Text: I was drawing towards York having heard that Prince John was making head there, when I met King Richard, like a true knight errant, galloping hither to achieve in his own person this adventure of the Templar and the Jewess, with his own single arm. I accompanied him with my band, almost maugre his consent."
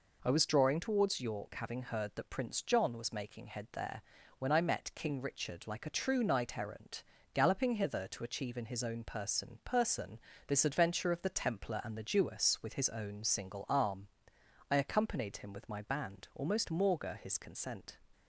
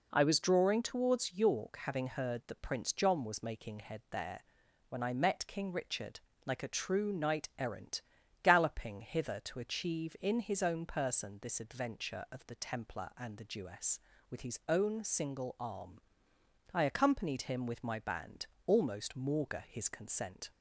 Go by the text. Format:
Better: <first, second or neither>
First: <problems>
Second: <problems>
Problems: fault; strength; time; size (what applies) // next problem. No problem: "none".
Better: second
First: says "person" twice; at 9.6 s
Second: none